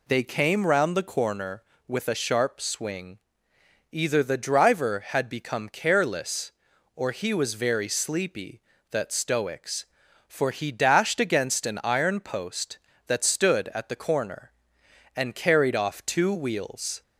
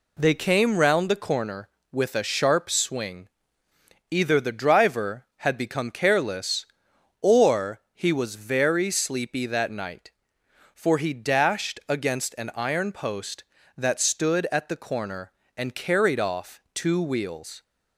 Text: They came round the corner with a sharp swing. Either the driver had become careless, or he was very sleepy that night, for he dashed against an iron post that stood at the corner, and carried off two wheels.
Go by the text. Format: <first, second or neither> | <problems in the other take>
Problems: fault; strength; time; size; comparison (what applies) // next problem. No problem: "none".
second | says "stoics" for "night"; at 9.1 s